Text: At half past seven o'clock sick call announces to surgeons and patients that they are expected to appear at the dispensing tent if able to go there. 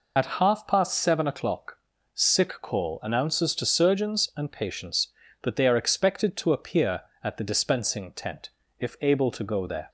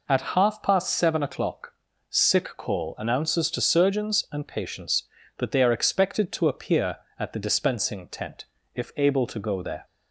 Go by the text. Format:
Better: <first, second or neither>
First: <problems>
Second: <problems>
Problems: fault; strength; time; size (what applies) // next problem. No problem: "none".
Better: second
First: loses the start of "At"; at 0.1 s; 45 ms // pauses between "o'clock" and "sick"; at 1.7 s; 0.38 s long // pauses between "tent" and "if"; slight; at 8.4 s; 0.30 s long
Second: pauses between "o'clock" and "sick"; at 1.7 s; 0.38 s long // pauses between "tent" and "if"; slight; at 8.4 s; 0.30 s long